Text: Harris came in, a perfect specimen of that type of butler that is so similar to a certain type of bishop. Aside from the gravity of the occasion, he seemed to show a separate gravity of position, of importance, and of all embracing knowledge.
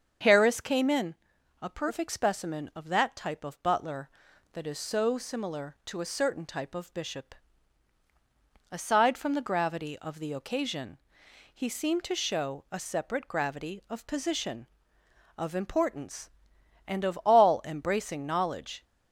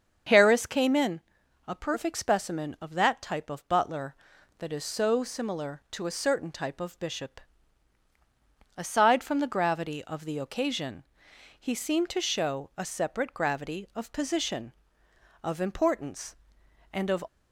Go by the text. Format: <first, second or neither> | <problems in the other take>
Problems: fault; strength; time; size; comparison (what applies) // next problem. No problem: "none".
first | starts louder than the rest; until 1.7 s; 7 dB; also in the first // stops before "all embracing knowledge"; at 17.2 s